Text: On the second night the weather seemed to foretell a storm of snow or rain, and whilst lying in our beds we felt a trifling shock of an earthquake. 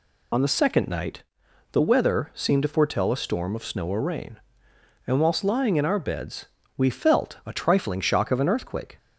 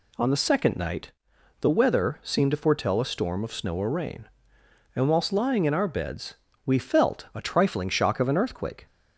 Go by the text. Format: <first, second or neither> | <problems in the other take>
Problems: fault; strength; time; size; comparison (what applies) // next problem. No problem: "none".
second | loses the start of "On"; at 0.3 s; 70 ms // pauses between "night" and "the"; noticeable; at 1.2 s; 0.50 s long; noticeable in the second // pauses between "beds" and "we"; slight; at 6.4 s; 0.30 s long; slight in the second